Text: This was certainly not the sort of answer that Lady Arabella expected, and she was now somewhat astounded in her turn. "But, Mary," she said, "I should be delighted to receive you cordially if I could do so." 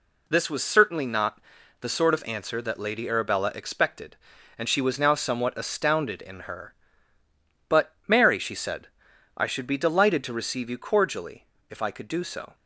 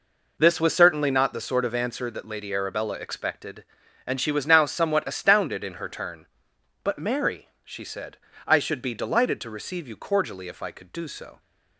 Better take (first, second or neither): second